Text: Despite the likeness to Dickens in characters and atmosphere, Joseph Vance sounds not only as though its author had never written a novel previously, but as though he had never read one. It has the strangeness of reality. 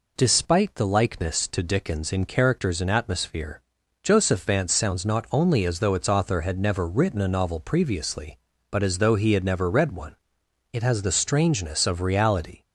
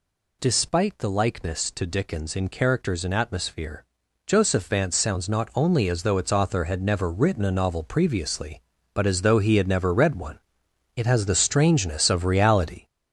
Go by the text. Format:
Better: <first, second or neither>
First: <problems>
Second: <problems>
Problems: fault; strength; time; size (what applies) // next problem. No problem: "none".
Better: first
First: none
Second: gets louder; throughout; 6 dB